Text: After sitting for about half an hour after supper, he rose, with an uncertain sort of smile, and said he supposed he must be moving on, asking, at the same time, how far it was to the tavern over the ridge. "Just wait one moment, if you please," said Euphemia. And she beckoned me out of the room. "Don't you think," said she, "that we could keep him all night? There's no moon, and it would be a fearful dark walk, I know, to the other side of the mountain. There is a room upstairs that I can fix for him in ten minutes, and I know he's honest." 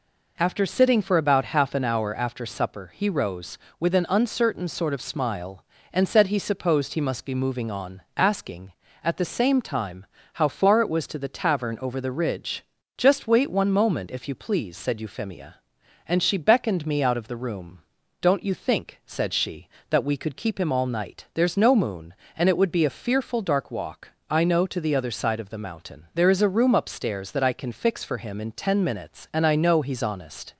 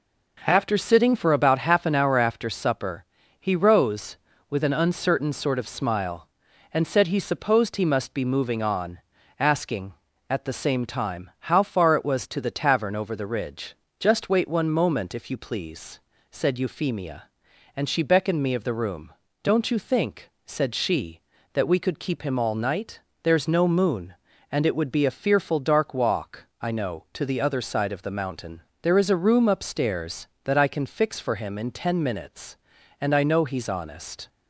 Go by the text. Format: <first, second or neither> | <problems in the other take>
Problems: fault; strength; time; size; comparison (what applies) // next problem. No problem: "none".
first | skips "out"; at 18.5 s